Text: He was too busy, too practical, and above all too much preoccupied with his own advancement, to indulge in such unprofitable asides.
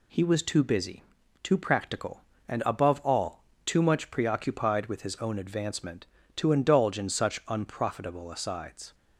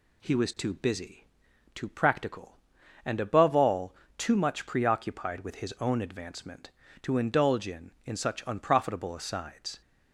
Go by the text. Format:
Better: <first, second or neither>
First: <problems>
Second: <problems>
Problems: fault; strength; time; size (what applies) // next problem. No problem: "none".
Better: first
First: pauses between "all" and "too"; slight; at 3.4 s; 0.22 s long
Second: pauses between "all" and "too"; slight; at 3.9 s; 0.24 s long // says "in" twice; at 8.0 s